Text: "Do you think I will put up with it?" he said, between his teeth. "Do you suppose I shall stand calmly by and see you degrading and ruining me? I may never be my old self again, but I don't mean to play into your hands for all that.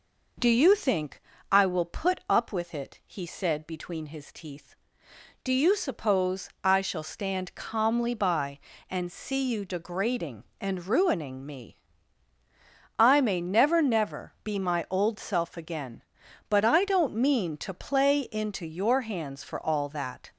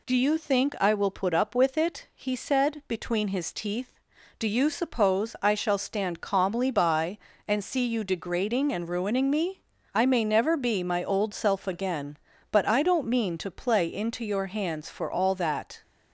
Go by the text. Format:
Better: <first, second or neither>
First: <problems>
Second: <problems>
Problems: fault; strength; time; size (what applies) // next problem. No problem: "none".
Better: second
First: pauses between "think" and "I"; slight; at 1.2 s; 0.30 s long // says "never" twice; at 13.8 s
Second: none